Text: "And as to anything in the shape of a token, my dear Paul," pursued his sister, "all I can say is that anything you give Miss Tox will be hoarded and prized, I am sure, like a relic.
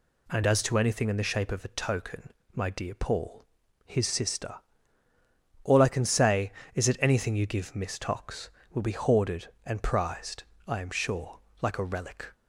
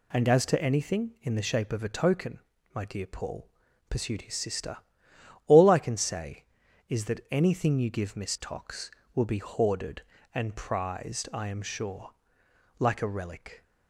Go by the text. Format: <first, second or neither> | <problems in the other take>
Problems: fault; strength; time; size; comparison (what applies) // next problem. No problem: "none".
second | skips "pursued"; at 3.6 s